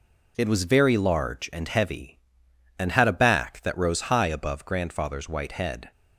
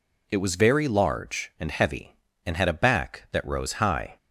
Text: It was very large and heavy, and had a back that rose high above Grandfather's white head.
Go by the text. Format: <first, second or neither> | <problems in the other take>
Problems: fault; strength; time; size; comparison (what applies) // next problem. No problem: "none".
first | stops before "above Grandfather's white head"; at 4.1 s